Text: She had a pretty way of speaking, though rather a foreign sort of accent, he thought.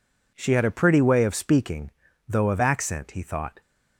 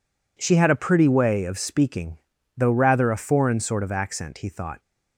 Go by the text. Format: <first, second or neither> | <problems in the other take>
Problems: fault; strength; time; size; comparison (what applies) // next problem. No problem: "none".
second | skips "rather a foreign sort"; at 2.5 s